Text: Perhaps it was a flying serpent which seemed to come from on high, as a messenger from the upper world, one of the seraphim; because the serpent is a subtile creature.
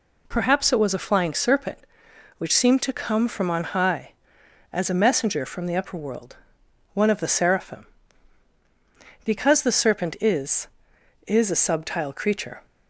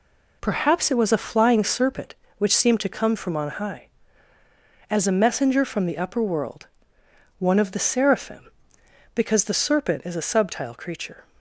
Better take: second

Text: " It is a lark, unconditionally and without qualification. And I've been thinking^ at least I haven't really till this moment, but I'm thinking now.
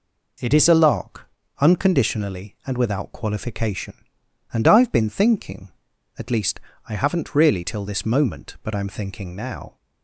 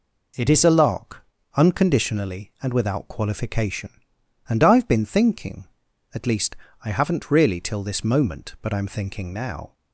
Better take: neither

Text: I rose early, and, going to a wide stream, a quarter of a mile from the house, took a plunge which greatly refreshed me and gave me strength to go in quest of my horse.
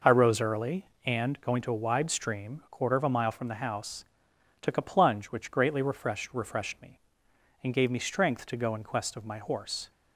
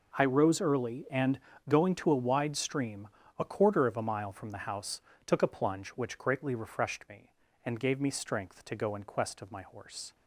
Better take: second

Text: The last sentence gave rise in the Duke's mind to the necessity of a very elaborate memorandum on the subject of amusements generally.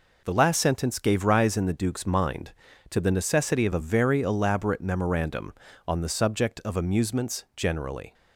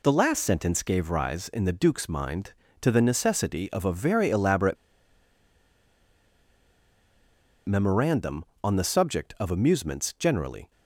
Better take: first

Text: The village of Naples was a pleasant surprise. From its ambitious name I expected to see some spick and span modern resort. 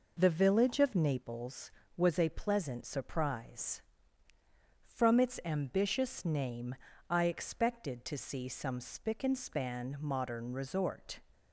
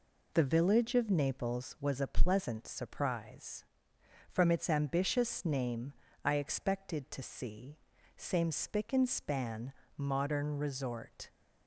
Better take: first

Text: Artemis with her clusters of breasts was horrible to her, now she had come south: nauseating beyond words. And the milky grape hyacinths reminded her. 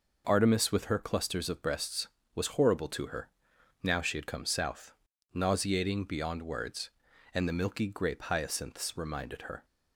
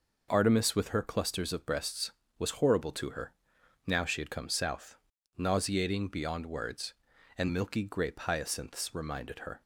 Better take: first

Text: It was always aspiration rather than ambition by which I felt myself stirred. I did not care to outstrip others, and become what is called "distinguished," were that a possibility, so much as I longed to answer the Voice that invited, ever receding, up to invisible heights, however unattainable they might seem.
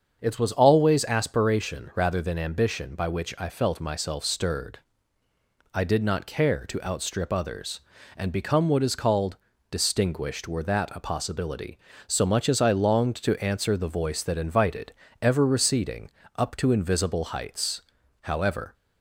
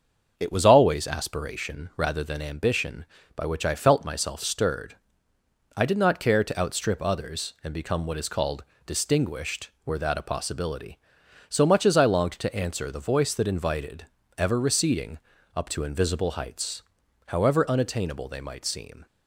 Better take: second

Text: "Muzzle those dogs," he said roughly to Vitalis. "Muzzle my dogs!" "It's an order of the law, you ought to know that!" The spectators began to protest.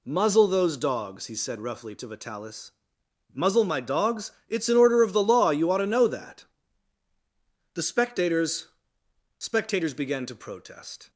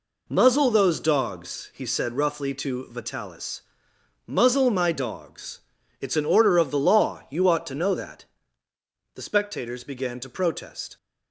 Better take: second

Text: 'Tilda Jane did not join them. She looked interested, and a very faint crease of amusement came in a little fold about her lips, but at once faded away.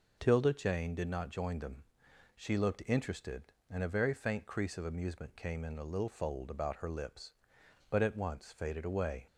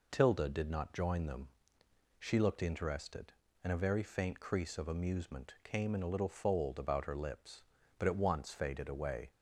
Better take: first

